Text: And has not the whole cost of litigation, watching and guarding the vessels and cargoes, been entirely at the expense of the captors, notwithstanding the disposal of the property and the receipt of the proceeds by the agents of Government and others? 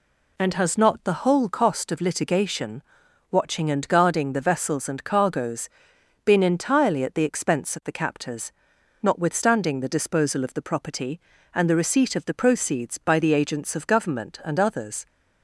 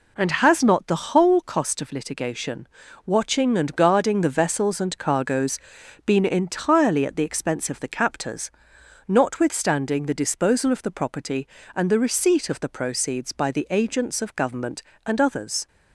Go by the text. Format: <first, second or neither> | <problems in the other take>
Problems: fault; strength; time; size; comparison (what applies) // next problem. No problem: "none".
neither | none